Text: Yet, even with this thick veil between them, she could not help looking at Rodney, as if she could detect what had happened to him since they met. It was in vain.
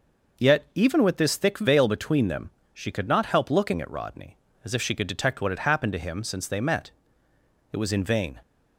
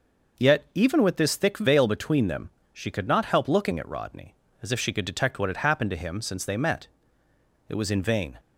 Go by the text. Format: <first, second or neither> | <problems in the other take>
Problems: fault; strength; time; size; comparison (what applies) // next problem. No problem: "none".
neither | none